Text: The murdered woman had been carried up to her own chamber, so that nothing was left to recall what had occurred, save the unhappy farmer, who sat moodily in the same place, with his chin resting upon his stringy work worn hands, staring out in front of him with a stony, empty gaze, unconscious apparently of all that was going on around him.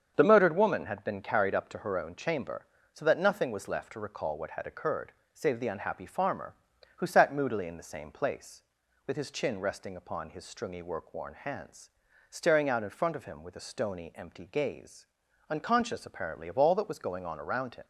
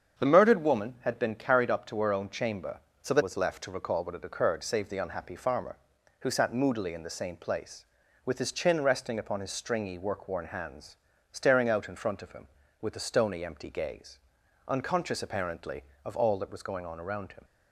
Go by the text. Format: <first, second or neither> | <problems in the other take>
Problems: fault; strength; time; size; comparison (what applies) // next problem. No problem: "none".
first | starts louder than the rest; strong; until 1.2 s; 7.5 dB; strong in the first // skips "nothing"; at 3.2 s